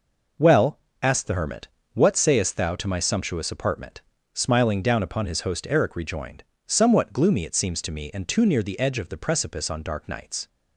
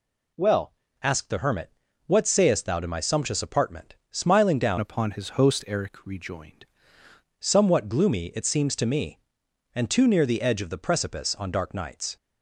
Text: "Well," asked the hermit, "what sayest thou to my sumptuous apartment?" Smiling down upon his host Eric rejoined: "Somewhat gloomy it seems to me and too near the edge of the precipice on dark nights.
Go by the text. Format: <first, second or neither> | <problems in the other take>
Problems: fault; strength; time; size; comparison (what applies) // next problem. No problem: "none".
first | changes voice from "upon" to "rejoined"; from 4.7 to 6.6 s; 1.9 s long